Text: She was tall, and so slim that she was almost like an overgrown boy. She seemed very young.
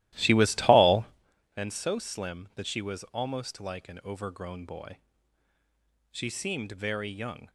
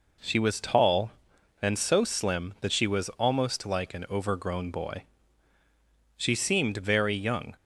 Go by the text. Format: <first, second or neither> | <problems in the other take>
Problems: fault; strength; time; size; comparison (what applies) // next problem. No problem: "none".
second | starts louder than the rest; strong; until 1.3 s; 15.5 dB